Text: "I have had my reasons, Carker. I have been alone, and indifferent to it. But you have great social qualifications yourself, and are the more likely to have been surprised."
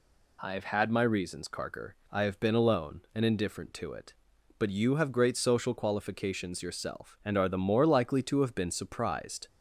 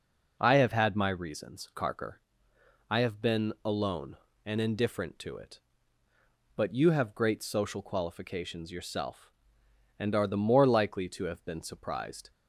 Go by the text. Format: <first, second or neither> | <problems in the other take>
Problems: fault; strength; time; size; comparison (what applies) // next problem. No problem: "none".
neither | none